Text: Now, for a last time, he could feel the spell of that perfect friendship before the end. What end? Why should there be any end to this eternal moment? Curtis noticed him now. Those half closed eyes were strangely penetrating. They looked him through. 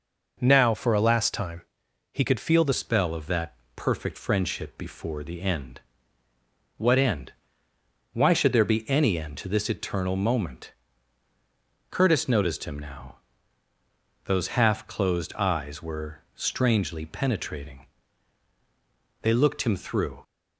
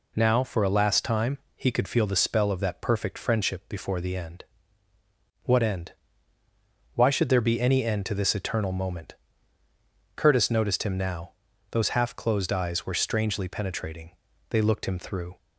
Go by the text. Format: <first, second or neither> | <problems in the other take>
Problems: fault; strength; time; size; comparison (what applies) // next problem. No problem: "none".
second | changes voice at "spell"; from 2.7 s on; 17.5 s long // pauses between "that" and "perfect"; slight; at 3.5 s; 0.22 s long